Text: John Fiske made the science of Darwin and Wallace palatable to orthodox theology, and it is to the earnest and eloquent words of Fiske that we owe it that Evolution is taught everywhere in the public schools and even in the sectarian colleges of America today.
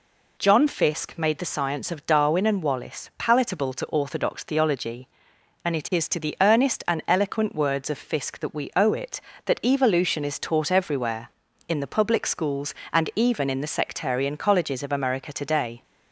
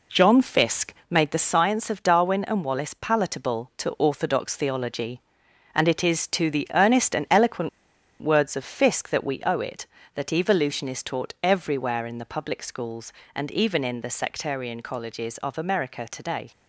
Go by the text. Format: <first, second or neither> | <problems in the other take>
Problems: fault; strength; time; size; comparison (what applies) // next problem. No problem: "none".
first | pauses between "Fiske" and "made"; slight; at 0.9 s; 0.16 s long // pauses between "eloquent" and "words"; noticeable; at 7.6 s; 0.53 s long